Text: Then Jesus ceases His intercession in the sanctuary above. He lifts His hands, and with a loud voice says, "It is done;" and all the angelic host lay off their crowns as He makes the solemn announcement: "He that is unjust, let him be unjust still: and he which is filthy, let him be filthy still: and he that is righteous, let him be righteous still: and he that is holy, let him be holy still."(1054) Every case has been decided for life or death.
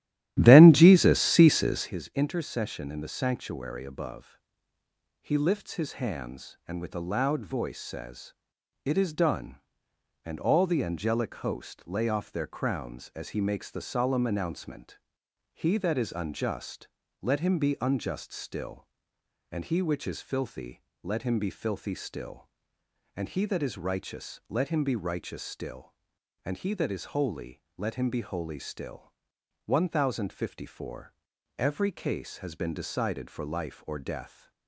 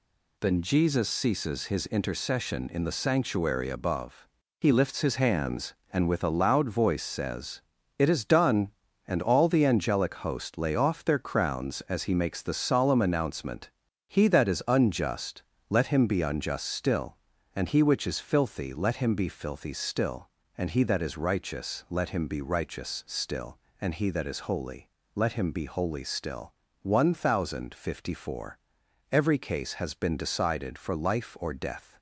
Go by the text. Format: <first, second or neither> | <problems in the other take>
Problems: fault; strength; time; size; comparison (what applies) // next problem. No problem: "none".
second | starts louder than the rest; strong; until 1.9 s; 13.5 dB